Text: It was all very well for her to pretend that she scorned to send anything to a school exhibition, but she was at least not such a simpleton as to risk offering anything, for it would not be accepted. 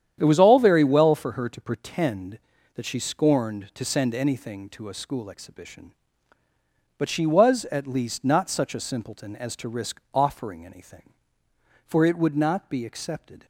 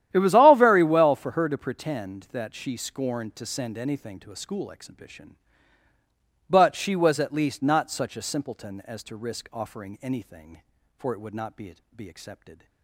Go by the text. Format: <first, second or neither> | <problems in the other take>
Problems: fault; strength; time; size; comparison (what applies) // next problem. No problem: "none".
first | starts louder than the rest; strong; until 1.1 s; 11.5 dB; strong in the first // says "be" twice; at 11.9 s